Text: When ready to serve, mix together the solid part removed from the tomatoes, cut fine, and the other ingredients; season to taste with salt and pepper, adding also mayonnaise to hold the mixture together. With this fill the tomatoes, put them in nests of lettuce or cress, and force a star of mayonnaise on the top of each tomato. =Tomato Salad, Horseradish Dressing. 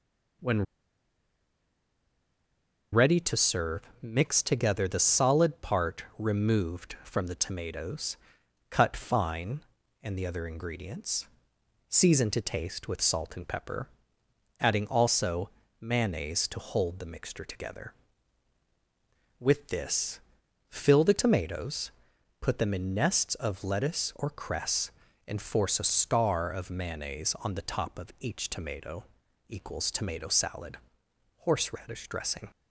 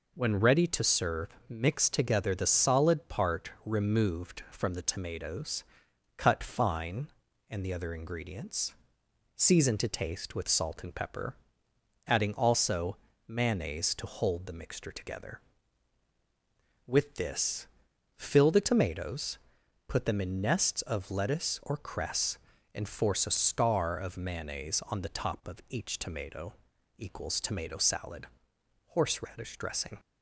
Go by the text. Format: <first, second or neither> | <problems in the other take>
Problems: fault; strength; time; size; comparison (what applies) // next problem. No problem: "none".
second | pauses between "When" and "ready"; strong; at 0.6 s; 2.2 s long // pauses between "part" and "removed"; slight; at 6.0 s; 0.16 s long; slight in the second // pauses between "also" and "mayonnaise"; slight; at 15.4 s; 0.32 s long; slight in the second // pauses between "this" and "fill"; noticeable; at 20.1 s; 0.50 s long; noticeable in the second